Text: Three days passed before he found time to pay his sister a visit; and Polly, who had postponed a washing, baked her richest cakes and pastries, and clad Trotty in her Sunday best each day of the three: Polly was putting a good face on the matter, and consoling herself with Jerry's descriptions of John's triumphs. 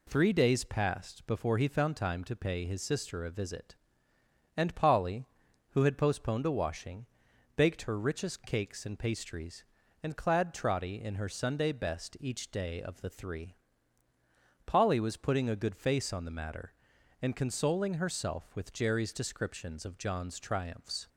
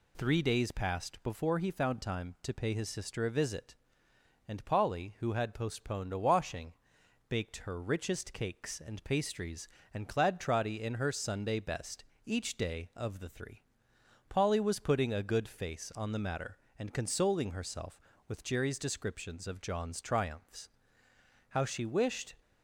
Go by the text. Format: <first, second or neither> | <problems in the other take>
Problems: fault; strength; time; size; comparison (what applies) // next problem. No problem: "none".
first | pauses between "best" and "each"; slight; at 12.0 s; 0.20 s long // goes on to say "How she wished"; noticeable; from 21.4 s on; 0.86 s long